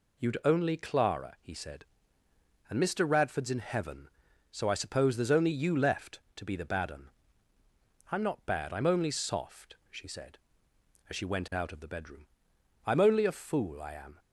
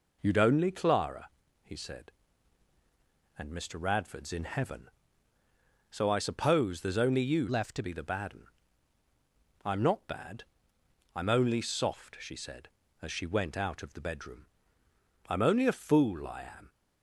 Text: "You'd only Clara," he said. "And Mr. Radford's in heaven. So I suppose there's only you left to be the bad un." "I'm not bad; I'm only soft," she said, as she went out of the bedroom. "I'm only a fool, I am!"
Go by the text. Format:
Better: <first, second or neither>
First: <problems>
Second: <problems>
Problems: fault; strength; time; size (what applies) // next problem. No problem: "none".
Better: first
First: none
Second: changes voice from "left" to "to"; from 7.4 to 7.8 s; 0.4 s long